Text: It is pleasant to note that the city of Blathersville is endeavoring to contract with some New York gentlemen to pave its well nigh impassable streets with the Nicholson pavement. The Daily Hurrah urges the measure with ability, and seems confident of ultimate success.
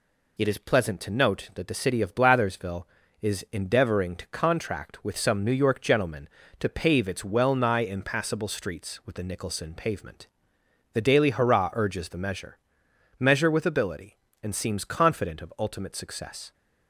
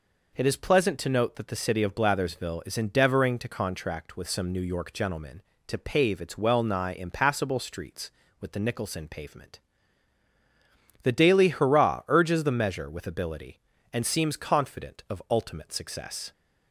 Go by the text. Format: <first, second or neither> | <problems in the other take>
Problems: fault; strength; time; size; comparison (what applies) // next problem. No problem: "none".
second | says "measure" twice; at 13.1 s